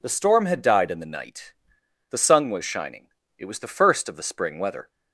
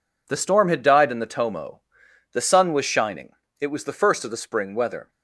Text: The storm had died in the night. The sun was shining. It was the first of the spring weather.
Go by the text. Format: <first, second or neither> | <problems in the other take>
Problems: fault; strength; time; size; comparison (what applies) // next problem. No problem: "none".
first | says "tomo" for "night"; at 1.2 s